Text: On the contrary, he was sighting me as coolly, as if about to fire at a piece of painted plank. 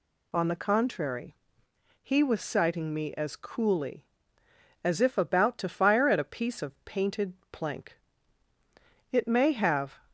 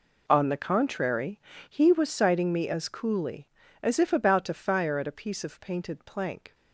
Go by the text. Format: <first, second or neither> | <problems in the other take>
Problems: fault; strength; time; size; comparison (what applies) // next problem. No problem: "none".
second | goes on to say "It may have"; noticeable; from 9.1 s on; 0.86 s long